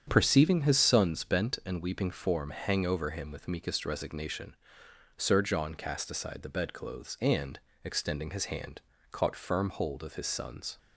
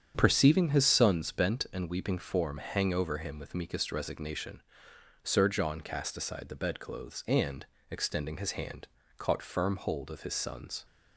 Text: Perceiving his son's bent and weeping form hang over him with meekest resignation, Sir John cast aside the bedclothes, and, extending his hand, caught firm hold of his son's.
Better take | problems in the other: neither | starts louder than the rest; strong; the same in both

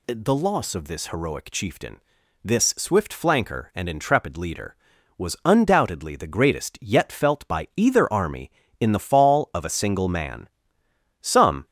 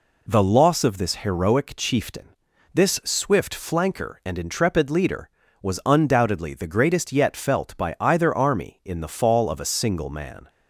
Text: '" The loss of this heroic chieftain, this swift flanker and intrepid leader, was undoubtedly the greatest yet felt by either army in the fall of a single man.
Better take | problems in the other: second | goes on to say "Some"; slight; from 11.2 s on; 0.44 s long

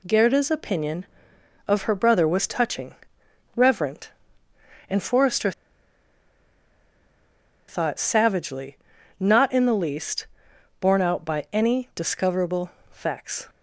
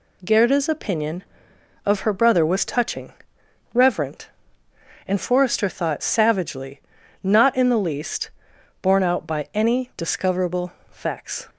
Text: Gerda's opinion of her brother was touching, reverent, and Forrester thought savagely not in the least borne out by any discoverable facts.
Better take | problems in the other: second | pauses between "Forrester" and "thought"; strong; at 5.5 s; 2.1 s long // pauses between "savagely" and "not"; at 8.7 s; 0.42 s long; also in the second // pauses between "least" and "borne"; noticeable; at 10.2 s; 0.52 s long; noticeable in the second // pauses between "discoverable" and "facts"; slight; at 12.6 s; 0.22 s long; slight in the second

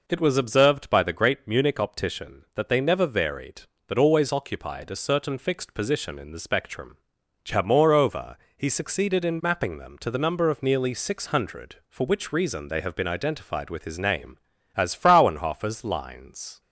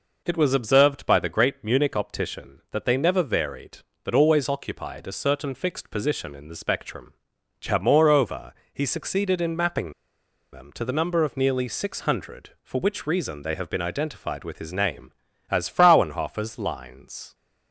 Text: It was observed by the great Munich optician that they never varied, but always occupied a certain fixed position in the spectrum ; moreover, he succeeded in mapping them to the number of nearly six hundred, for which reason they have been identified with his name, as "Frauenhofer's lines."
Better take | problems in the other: first | pauses between "mapping" and "them"; noticeable; at 9.9 s; 0.59 s long

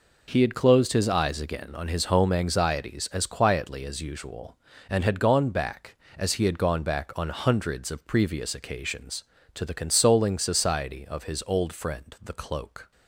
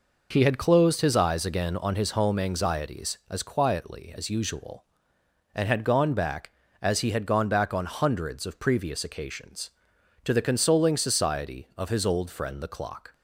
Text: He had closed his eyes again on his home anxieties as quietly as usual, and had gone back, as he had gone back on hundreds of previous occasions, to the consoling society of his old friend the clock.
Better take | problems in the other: second | says "cloak" for "clock"; at 12.3 s

